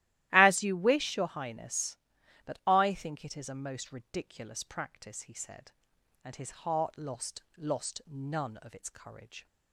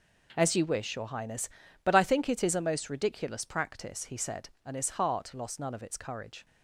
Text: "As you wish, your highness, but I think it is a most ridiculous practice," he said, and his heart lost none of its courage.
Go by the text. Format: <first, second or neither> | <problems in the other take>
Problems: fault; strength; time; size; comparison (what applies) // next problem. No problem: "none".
second | starts louder than the rest; strong; until 1.3 s; 15 dB // says "lost" twice; at 7.5 s